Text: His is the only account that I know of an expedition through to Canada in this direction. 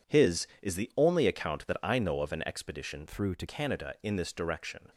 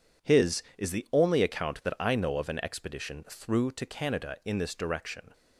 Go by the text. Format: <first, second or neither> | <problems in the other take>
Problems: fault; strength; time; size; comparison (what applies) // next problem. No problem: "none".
second | changes voice from "through" to "to"; from 3.0 to 3.4 s; 0.4 s long